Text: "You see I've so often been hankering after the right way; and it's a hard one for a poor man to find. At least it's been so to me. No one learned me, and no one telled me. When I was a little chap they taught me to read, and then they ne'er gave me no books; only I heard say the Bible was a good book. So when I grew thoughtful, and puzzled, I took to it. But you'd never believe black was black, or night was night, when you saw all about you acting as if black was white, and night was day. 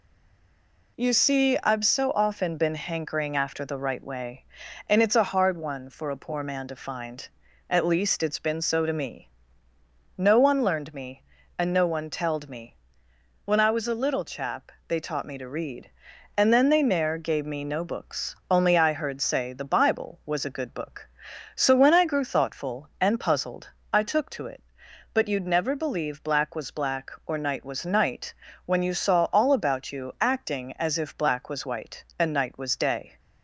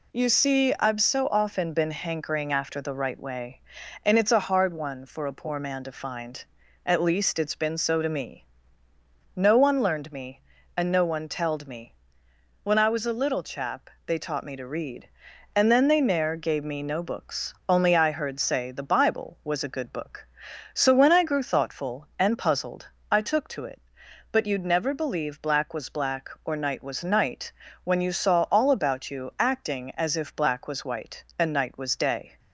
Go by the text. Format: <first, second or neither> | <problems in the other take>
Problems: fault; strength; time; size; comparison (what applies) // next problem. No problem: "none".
second | stays silent before the first word; slight; until 0.9 s; 0.9 s long // pauses between "chap" and "they"; slight; at 14.7 s; 0.16 s long; slight in the second